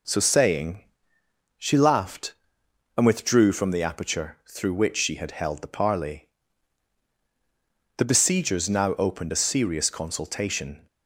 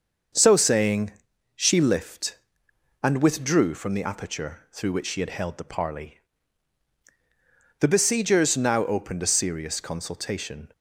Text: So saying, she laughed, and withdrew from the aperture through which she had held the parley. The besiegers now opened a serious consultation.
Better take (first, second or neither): first